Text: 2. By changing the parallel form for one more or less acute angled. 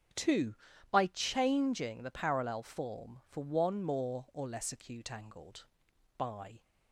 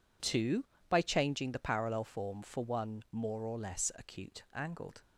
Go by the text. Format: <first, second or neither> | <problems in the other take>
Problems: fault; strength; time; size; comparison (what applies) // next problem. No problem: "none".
second | starts louder than the rest; strong; until 1.5 s; 8 dB // goes on to say "By"; slight; from 6.1 s on; 0.44 s long